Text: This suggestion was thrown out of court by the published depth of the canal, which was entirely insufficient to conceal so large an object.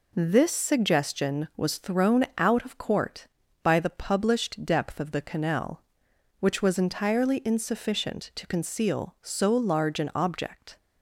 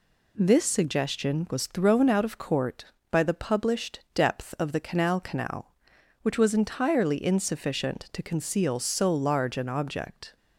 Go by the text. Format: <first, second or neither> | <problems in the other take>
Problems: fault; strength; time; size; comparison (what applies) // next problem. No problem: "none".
first | says "canal" twice; at 5.1 s